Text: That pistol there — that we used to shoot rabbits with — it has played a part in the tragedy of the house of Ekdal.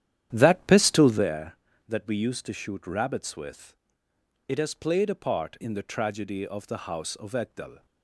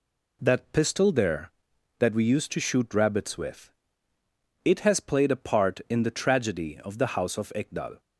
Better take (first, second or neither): second